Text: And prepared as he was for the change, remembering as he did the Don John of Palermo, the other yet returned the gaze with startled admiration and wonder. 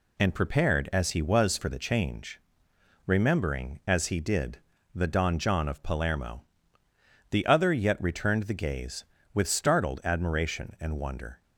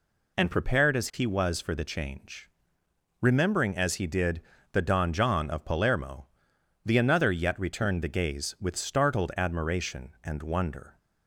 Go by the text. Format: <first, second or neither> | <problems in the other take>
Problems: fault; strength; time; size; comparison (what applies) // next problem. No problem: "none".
first | pauses between "did" and "the"; slight; at 4.3 s; 0.32 s long; slight in the first // says "another" for "other"; at 6.9 s